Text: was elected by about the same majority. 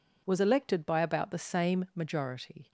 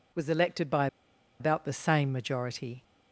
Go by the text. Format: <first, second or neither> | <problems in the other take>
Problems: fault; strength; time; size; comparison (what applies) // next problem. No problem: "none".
first | pauses between "by" and "about"; noticeable; at 0.8 s; 0.53 s long